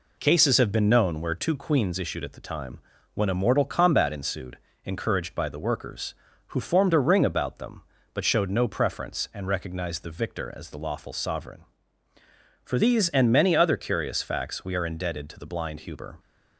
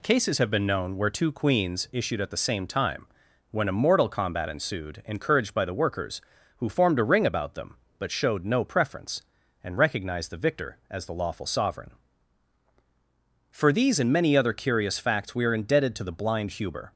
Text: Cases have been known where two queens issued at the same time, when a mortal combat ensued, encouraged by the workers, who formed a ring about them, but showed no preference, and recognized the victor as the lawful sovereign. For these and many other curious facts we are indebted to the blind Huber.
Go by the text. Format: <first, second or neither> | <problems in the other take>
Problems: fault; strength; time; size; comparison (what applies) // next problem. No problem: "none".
second | skips "same"; at 2.3 s